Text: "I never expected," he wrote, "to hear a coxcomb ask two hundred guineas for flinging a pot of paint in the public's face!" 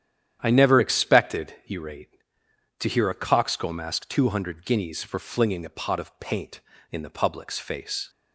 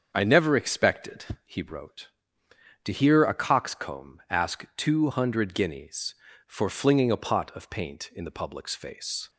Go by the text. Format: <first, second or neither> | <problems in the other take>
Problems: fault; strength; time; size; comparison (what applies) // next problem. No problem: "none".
second | starts louder than the rest; strong; until 1.4 s; 10 dB; also in the second // says "rate" for "wrote"; at 1.7 s